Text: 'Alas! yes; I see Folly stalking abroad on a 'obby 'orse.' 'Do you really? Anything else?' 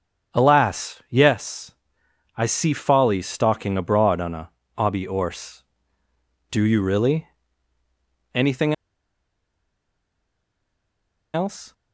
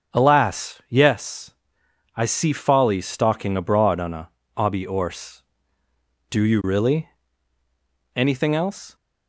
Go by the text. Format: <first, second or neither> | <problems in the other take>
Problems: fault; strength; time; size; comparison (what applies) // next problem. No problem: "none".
second | starts louder than the rest; strong; until 1.4 s; 7 dB; also in the second // pauses between "a" and "obby"; slight; at 4.4 s; 0.26 s long; slight in the second // pauses between "Anything" and "else"; strong; at 8.7 s; 2.6 s long